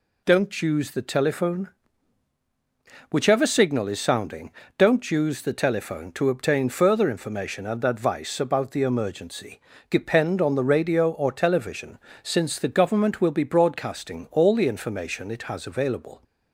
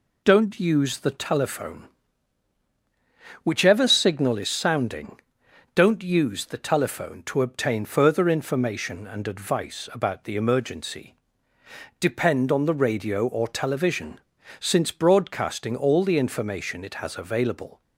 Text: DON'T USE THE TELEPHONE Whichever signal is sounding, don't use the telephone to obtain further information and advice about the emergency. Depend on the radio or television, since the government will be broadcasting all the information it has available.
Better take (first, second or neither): first